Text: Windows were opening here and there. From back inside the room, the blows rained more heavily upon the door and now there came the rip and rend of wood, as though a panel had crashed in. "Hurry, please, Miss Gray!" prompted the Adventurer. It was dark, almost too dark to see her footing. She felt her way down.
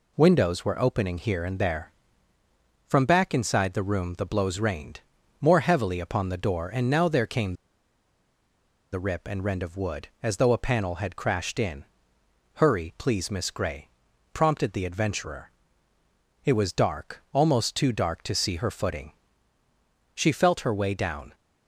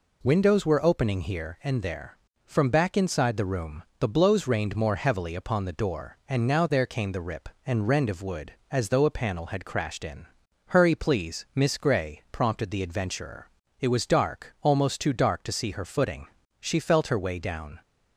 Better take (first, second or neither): second